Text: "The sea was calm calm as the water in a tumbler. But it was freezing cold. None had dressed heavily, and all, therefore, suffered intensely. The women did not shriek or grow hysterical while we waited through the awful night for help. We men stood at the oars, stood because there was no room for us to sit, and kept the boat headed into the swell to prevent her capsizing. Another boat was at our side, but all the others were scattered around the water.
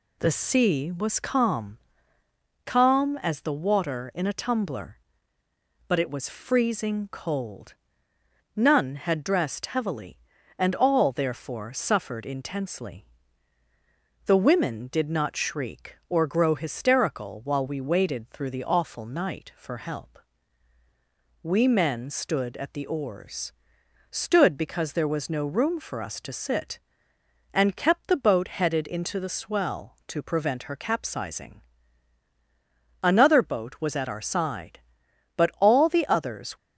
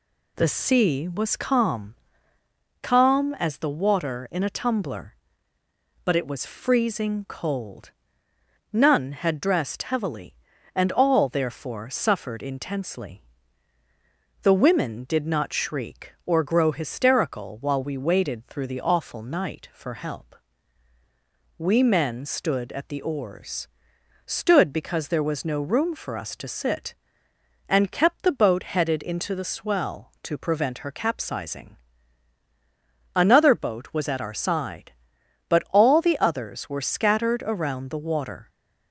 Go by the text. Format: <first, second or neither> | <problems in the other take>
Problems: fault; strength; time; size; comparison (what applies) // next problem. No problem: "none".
second | pauses between "calm" and "calm"; noticeable; at 1.7 s; 0.88 s long; noticeable in the second // stops before "were scattered around the water"; at 36.5 s